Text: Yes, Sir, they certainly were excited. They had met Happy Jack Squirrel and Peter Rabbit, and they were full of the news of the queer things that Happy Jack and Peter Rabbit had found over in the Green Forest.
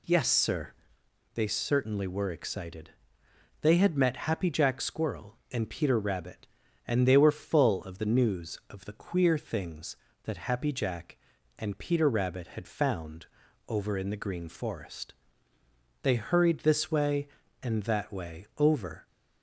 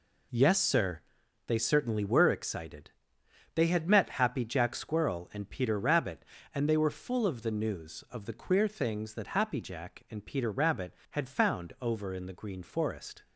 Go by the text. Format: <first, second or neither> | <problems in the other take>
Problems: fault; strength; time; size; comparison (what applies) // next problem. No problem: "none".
second | pauses between "found" and "over"; at 13.2 s; 0.42 s long // goes on to say "They hurried this way and that way over"; strong; from 16.0 s on; 3.0 s long